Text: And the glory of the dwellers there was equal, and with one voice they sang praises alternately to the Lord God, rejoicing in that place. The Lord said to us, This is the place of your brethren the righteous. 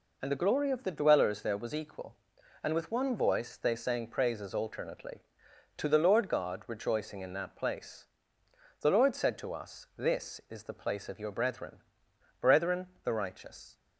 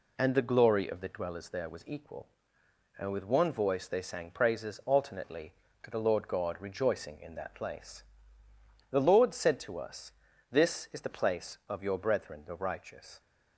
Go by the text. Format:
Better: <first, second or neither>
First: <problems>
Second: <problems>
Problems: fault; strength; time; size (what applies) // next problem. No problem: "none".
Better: second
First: says "brethren" twice; at 12.3 s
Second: none